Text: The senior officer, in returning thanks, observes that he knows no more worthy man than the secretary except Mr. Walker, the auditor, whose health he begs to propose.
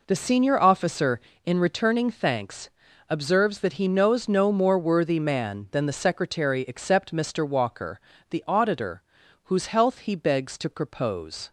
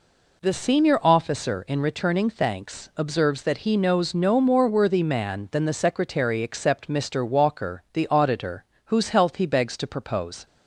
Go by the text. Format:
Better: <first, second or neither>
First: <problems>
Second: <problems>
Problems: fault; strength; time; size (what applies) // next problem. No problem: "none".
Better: neither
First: none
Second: none